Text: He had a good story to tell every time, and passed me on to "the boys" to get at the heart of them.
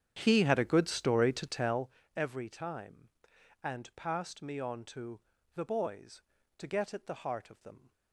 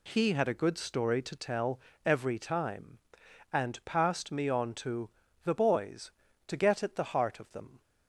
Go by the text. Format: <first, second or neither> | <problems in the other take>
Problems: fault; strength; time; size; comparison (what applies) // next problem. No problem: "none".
second | starts louder than the rest; strong; until 1.9 s; 9 dB // pauses between "tell" and "every"; slight; at 1.9 s; 0.24 s long; slight in the second // pauses between "to" and "the"; slight; at 5.1 s; 0.34 s long; slight in the second